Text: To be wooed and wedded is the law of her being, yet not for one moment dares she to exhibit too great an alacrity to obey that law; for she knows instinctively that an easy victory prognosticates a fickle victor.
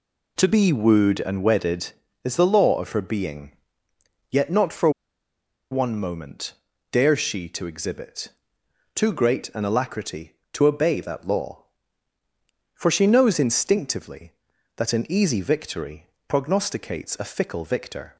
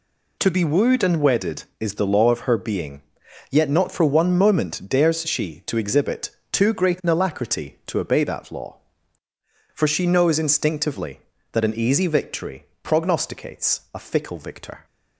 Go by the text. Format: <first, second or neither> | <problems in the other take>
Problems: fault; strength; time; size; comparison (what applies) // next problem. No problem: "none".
second | pauses between "for" and "one"; noticeable; at 4.8 s; 0.81 s long // pauses between "moment" and "dares"; at 6.5 s; 0.38 s long // pauses between "exhibit" and "too"; noticeable; at 8.2 s; 0.66 s long; slight in the second // pauses between "victory" and "prognosticates"; slight; at 16.0 s; 0.22 s long; slight in the second